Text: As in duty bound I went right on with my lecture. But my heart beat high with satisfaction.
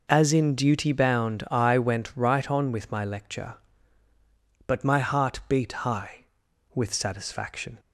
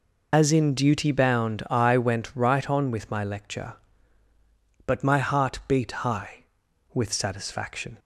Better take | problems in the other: first | loses the start of "As"; at 0.3 s; 45 ms

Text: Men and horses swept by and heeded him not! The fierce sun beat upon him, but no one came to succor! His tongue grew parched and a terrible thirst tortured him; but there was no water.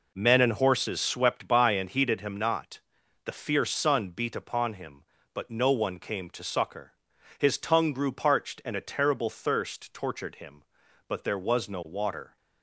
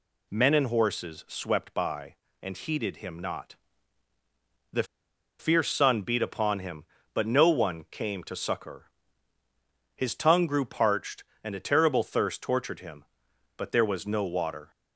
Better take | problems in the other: first | pauses between "The" and "fierce"; noticeable; at 4.8 s; 0.55 s long

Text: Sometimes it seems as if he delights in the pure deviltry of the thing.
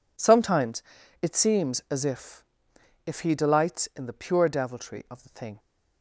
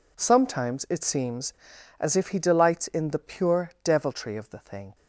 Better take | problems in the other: second | pauses between "Sometimes" and "it"; at 0.8 s; 0.39 s long // says "if" twice; at 3.0 s

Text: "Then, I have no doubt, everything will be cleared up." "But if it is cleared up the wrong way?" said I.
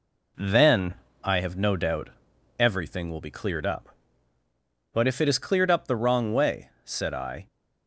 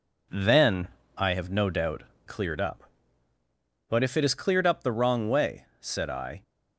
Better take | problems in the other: first | skips "everything will be"; at 2.1 s

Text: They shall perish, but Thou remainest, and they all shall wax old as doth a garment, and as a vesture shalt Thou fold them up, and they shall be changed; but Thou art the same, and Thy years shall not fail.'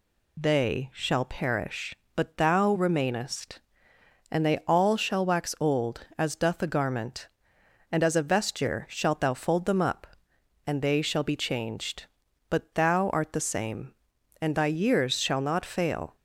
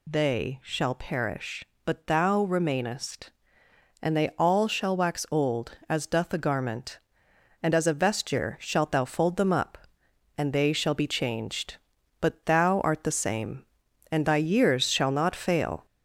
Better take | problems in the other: first | gets louder; slight; throughout; 2.5 dB

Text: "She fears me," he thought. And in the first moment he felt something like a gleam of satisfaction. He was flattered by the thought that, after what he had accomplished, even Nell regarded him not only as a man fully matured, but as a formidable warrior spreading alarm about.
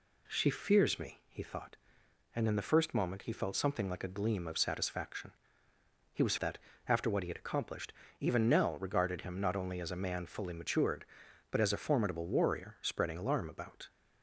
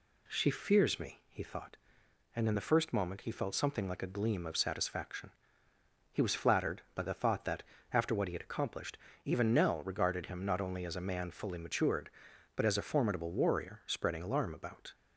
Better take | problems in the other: second | skips "flattered by the thought"; at 6.3 s

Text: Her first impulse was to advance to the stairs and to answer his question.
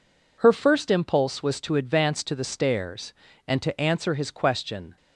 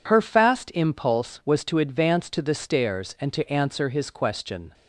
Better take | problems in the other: first | says "fast" for "first"; at 0.2 s

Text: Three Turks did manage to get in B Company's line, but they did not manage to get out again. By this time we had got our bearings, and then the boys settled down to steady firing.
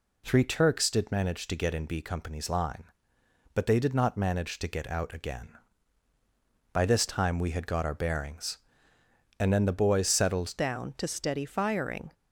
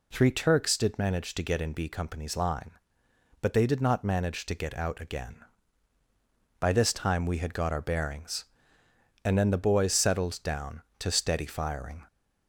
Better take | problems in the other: second | changes voice at "down"; from 10.5 s on; 1.6 s long

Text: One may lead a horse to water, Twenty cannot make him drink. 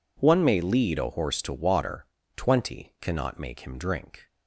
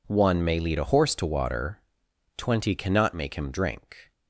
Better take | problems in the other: neither | none

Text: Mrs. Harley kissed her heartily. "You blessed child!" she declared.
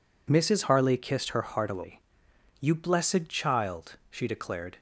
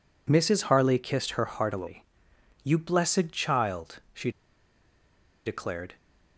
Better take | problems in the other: first | pauses between "she" and "declared"; at 4.3 s; 1.1 s long

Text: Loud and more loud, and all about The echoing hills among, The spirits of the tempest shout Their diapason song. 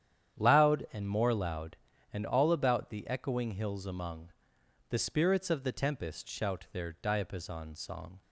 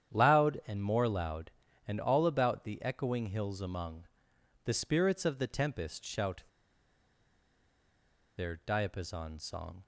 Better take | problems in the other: first | starts louder than the rest; strong; until 1.1 s; 9.5 dB; strong in the first // pauses between "shout" and "Their"; strong; at 6.4 s; 1.9 s long

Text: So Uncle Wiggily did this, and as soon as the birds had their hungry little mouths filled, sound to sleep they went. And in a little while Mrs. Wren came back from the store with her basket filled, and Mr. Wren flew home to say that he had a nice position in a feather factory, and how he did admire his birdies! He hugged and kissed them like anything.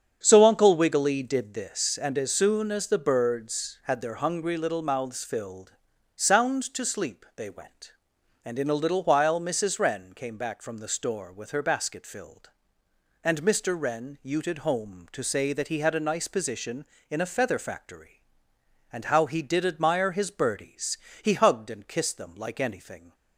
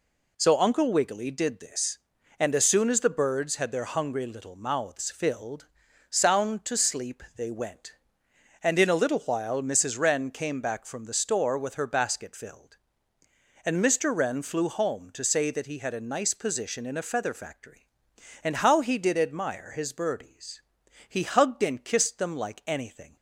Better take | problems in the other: second | starts louder than the rest; strong; until 1.2 s; 7.5 dB // says "uted" for "flew"; at 14.2 s

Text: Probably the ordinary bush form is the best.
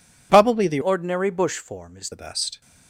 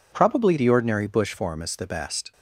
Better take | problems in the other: second | changes voice from "ordinary" to "is"; from 0.8 to 2.1 s; 1.3 s long

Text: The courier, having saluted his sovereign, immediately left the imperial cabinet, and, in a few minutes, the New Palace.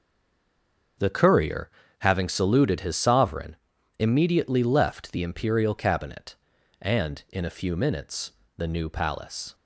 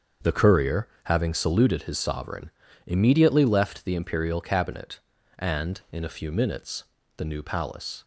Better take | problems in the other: second | stays silent before the first word; until 0.9 s; 0.9 s long // starts louder than the rest; until 2.2 s; 6.5 dB; also in the second

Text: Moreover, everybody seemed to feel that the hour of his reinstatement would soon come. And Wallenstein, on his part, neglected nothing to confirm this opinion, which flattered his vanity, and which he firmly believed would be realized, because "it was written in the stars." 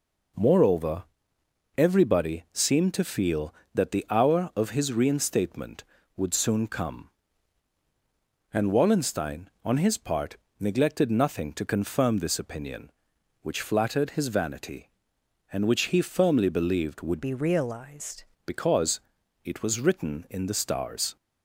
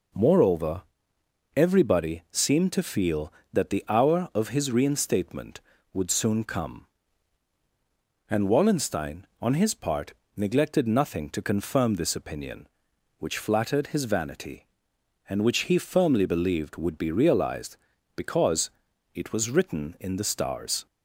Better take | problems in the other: second | changes voice from "be" to "realized"; from 17.2 to 18.2 s; 1.0 s long // pauses between "because" and "it"; at 18.9 s; 0.44 s long; also in the second

